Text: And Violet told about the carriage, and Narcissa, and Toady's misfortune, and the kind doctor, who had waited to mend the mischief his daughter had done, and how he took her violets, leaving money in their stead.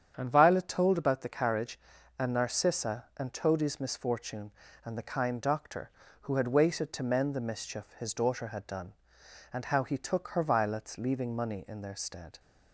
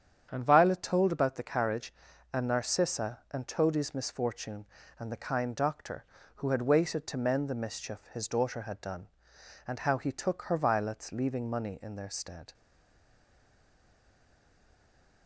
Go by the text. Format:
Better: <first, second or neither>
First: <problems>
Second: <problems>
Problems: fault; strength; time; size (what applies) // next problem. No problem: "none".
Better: first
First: starts louder than the rest; strong; until 1.1 s; 8.5 dB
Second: starts louder than the rest; strong; until 1.3 s; 8.5 dB // stays silent after the last word; strong; from 12.5 s on; 2.7 s long